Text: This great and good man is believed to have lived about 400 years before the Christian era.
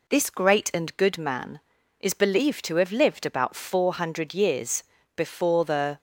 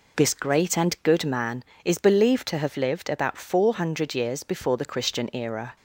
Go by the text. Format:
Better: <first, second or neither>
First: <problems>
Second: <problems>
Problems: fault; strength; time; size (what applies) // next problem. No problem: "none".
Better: second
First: pauses between "years" and "before"; slight; at 4.8 s; 0.32 s long // stops before "Christian era"; at 5.9 s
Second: none